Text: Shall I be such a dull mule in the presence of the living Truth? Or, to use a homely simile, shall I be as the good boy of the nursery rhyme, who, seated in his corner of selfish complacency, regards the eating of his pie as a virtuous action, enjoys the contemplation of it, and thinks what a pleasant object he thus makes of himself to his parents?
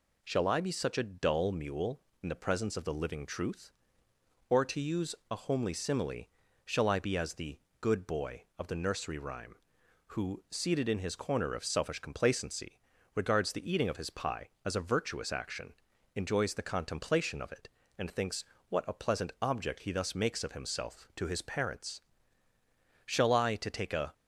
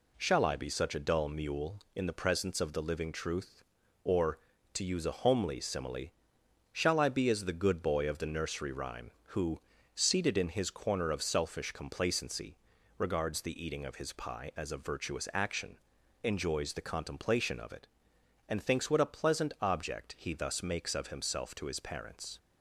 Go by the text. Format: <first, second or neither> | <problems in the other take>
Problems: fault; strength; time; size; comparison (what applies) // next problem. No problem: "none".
second | pauses between "use" and "a"; slight; at 5.1 s; 0.16 s long // pauses between "the" and "good"; slight; at 7.5 s; 0.20 s long // pauses between "thinks" and "what"; slight; at 18.4 s; 0.26 s long // goes on to say "Shall I to take a"; noticeable; from 23.0 s on; 1.0 s long